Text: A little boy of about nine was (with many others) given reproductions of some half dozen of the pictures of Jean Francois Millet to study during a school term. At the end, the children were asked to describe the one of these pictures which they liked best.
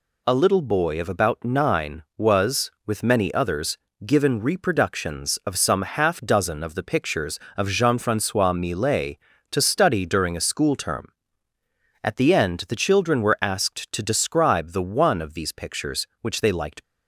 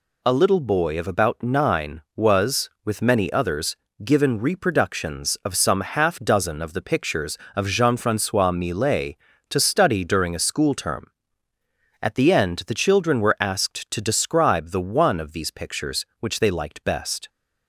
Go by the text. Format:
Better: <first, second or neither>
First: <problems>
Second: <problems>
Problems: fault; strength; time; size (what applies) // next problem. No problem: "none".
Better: second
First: stops before "best"; at 16.8 s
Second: none